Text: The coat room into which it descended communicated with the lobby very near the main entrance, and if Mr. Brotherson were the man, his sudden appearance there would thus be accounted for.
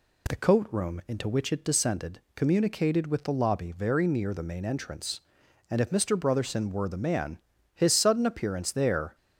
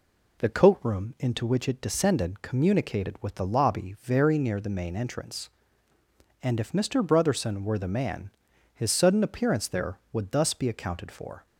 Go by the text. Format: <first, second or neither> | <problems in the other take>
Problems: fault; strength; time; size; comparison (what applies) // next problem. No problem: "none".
second | pauses between "descended" and "communicated"; slight; at 2.1 s; 0.16 s long // stops before "would thus be accounted for"; at 9.1 s